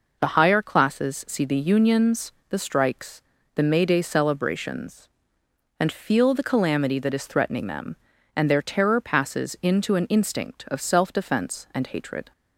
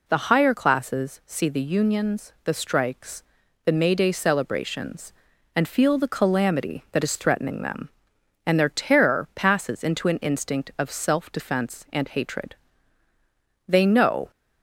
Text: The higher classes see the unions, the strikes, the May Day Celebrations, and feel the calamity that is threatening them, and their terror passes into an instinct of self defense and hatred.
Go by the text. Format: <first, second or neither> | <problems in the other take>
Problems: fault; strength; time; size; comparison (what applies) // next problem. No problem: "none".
first | goes on to say "They know"; noticeable; from 13.6 s on; 0.64 s long